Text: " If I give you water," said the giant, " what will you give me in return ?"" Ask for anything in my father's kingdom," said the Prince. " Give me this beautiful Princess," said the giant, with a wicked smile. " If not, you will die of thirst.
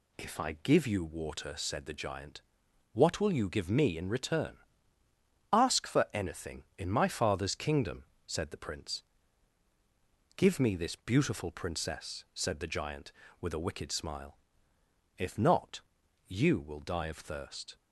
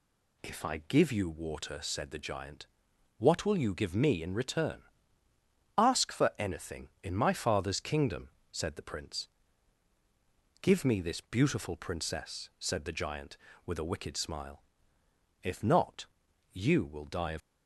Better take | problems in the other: first | stops before "thirst"; at 17.4 s

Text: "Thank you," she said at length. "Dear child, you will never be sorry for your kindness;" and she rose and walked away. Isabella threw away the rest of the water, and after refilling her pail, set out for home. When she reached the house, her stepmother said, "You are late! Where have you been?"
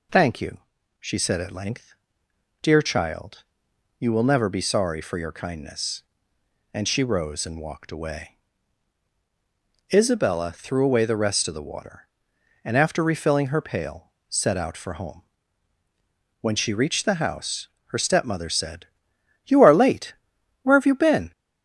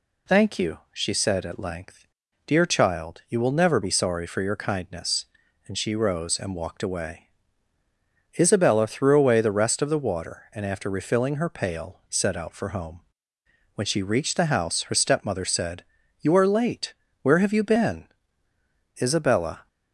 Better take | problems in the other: first | goes on to say "Isabella"; noticeable; from 19.0 s on; 0.66 s long

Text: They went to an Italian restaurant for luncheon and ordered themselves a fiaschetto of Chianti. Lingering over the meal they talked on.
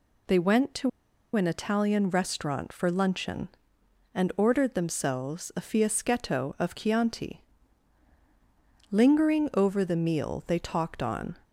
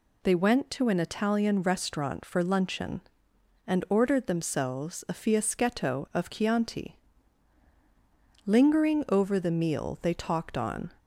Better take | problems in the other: second | pauses between "to" and "an"; noticeable; at 0.8 s; 0.46 s long

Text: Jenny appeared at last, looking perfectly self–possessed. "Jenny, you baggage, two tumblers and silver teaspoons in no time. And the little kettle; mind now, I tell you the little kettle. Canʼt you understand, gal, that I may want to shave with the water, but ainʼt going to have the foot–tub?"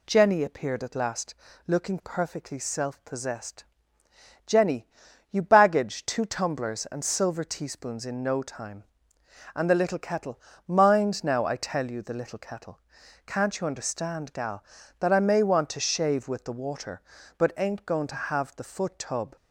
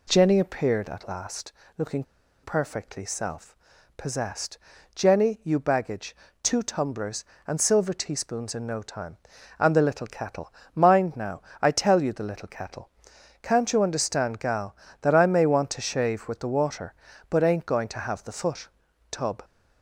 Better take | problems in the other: first | pauses between "looking" and "perfectly"; at 2.0 s; 0.41 s long

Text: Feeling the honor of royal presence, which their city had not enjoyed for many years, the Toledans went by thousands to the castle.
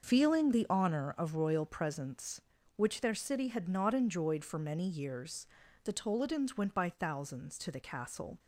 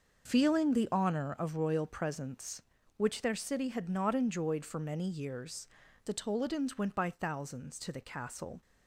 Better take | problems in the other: neither | starts louder than the rest; the same in both

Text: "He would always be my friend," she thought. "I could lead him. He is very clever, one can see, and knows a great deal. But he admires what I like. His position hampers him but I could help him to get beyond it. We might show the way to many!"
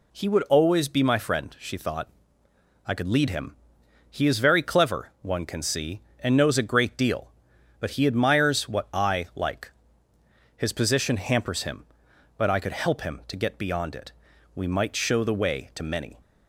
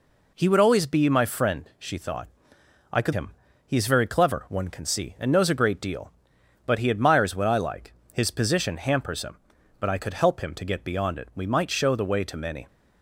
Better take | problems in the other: first | skips "lead"; at 3.1 s

